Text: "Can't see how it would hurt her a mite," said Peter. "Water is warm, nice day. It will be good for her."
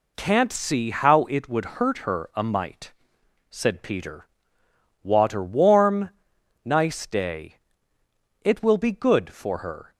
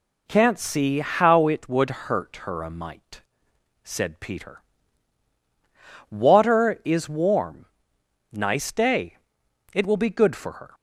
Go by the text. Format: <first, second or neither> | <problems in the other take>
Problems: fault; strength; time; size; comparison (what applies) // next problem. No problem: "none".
second | skips "is"; at 5.4 s